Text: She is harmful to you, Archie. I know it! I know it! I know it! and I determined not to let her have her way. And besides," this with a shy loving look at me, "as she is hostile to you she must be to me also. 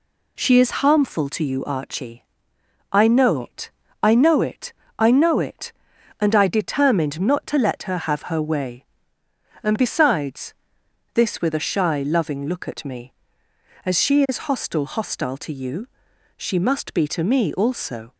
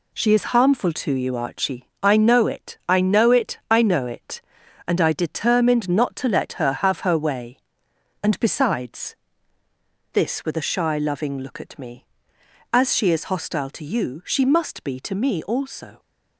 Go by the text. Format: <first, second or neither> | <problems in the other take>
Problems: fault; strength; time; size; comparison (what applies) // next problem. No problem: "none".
second | says "hostile" twice; at 14.8 s // pauses between "you" and "she"; noticeable; at 15.8 s; 0.52 s long